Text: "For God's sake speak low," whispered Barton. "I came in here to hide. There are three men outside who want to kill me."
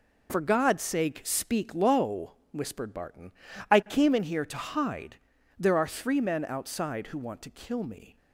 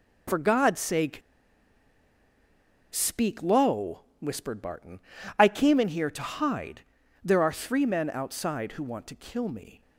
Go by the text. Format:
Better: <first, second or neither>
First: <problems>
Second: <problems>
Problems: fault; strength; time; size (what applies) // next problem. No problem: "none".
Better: first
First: none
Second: pauses between "sake" and "speak"; strong; at 1.2 s; 1.7 s long